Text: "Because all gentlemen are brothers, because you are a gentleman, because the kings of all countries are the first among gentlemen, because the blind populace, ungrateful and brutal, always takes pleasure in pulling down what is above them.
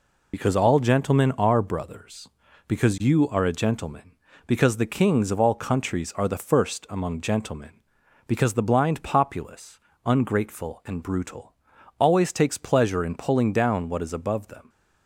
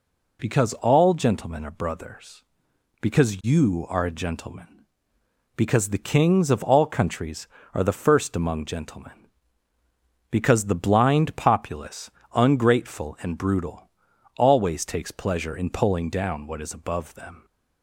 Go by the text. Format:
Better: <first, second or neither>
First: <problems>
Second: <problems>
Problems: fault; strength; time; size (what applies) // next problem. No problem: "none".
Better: second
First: loses the start of "Because"; at 0.3 s; 45 ms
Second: none